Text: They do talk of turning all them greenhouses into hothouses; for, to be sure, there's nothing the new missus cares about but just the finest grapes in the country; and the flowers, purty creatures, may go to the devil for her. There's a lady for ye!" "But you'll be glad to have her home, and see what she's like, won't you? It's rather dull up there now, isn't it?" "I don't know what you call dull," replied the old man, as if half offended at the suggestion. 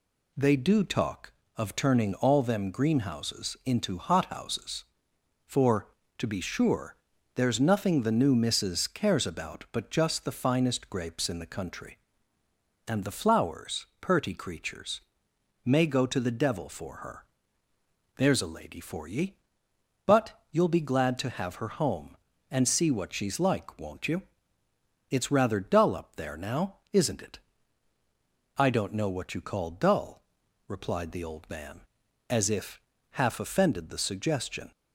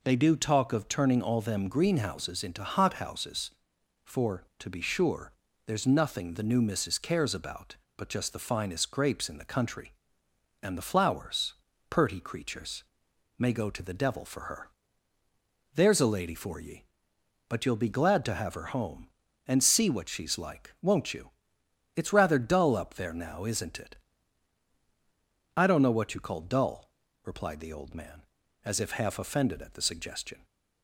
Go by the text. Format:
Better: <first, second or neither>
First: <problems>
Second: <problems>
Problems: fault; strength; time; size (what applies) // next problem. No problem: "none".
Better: second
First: pauses between "But" and "you'll"; slight; at 20.3 s; 0.18 s long // pauses between "if" and "half"; slight; at 32.8 s; 0.30 s long // skips "at"; at 33.9 s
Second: none